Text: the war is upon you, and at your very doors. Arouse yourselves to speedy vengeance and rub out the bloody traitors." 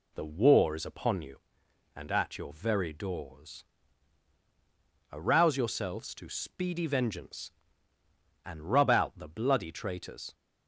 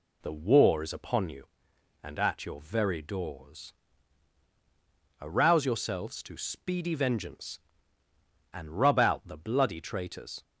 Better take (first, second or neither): neither